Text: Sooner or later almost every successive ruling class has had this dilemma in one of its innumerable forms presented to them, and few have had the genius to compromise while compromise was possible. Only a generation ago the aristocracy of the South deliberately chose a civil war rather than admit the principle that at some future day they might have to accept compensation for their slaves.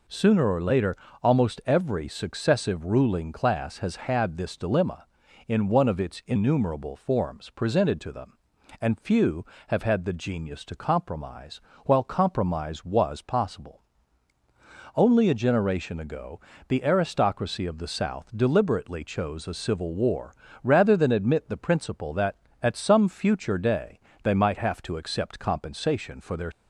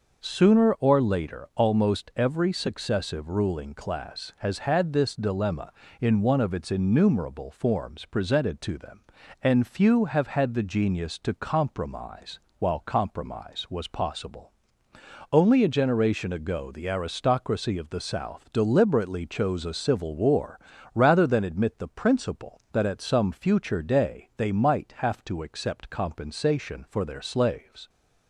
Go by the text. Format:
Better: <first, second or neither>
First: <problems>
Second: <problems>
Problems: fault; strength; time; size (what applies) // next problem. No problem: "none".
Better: second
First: pauses between "later" and "almost"; slight; at 0.9 s; 0.28 s long // pauses between "compromise" and "while"; slight; at 11.5 s; 0.26 s long // pauses between "ago" and "the"; slight; at 16.3 s; 0.30 s long // pauses between "war" and "rather"; slight; at 20.3 s; 0.30 s long // pauses between "day" and "they"; slight; at 23.9 s; 0.24 s long // stops before "slaves"; at 26.5 s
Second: pauses between "compromise" and "while"; slight; at 12.3 s; 0.22 s long // pauses between "war" and "rather"; slight; at 20.5 s; 0.34 s long